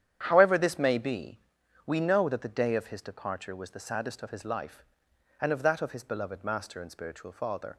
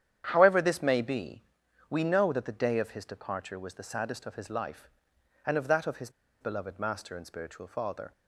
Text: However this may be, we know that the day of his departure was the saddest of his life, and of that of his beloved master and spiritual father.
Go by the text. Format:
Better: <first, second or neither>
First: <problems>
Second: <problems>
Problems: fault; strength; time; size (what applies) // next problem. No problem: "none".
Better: first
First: starts louder than the rest; strong; until 1.2 s; 9.5 dB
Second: starts louder than the rest; strong; until 1.3 s; 9.5 dB // pauses between "his" and "beloved"; slight; at 6.0 s; 0.31 s long